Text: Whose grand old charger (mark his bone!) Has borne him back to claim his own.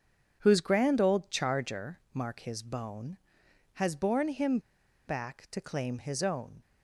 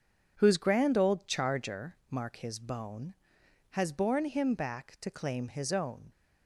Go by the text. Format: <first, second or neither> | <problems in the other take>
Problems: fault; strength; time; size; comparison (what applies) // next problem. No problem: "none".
second | pauses between "him" and "back"; noticeable; at 4.5 s; 0.50 s long